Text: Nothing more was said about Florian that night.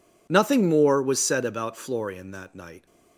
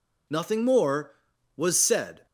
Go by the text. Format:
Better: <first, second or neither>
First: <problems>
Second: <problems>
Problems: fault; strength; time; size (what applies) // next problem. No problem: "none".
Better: first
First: none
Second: stops before "about Florian that night"; at 2.2 s